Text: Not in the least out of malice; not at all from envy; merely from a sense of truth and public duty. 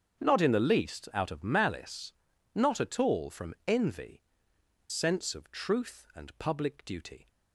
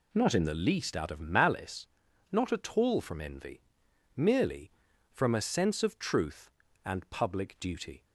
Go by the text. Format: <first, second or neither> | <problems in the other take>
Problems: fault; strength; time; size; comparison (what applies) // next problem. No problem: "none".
second | starts louder than the rest; strong; until 1.2 s; 7.5 dB // skips "merely from a"; at 4.5 s